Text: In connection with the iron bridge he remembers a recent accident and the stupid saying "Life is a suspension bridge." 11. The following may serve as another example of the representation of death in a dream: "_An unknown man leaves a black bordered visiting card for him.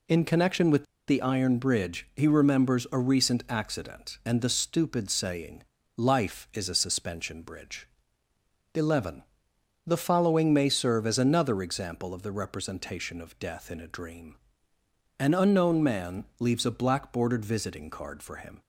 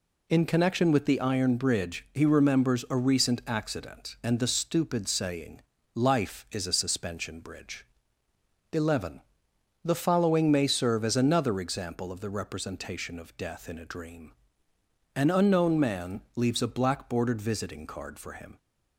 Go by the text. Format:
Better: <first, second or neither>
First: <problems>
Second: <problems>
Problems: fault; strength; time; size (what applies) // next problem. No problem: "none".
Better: second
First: pauses between "with" and "the"; slight; at 0.8 s; 0.25 s long // pauses between "saying" and "Life"; slight; at 5.6 s; 0.36 s long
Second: pauses between "saying" and "Life"; slight; at 5.5 s; 0.36 s long